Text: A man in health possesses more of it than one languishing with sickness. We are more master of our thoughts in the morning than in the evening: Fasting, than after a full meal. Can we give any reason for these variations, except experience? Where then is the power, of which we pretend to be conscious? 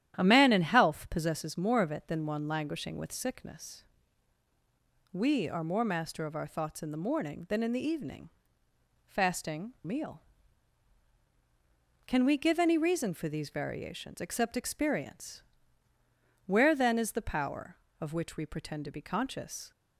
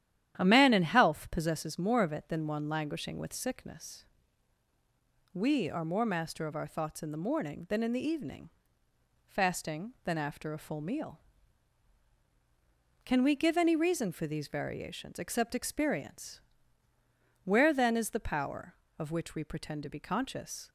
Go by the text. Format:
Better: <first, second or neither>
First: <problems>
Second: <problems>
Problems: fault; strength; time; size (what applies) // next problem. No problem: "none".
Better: second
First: starts louder than the rest; strong; until 1.1 s; 11 dB // skips "than after a full"; at 9.7 s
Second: starts louder than the rest; strong; until 1.4 s; 11 dB